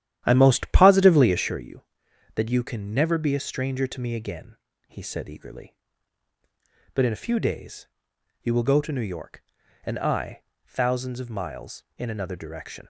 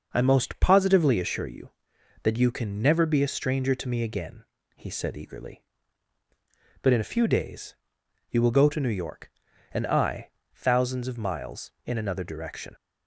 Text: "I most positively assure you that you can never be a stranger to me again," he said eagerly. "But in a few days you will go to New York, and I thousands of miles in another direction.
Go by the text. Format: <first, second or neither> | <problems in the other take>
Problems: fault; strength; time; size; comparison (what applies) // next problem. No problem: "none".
second | starts louder than the rest; strong; until 1.7 s; 11 dB // pauses between "days" and "you"; noticeable; at 7.8 s; 0.56 s long; noticeable in the second // pauses between "I" and "thousands"; slight; at 10.4 s; 0.24 s long; slight in the second